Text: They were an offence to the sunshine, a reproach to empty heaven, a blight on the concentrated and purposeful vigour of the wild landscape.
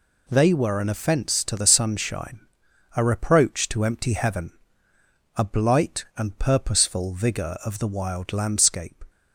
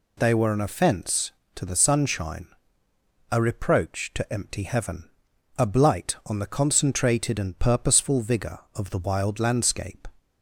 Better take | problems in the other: second | skips "on the concentrated"; at 6.1 s

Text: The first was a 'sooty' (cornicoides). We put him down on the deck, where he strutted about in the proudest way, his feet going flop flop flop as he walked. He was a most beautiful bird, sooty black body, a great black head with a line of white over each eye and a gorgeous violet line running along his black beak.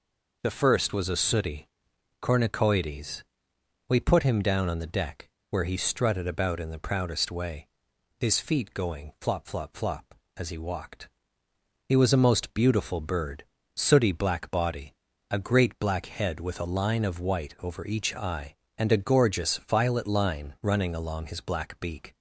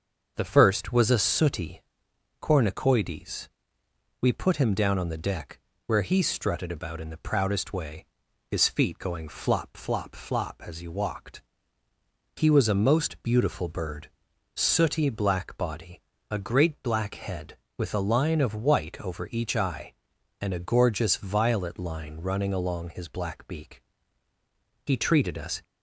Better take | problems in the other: first | starts louder than the rest; until 1.3 s; 6.5 dB // goes on to say "He treated us"; noticeable; from 24.8 s on; 0.78 s long

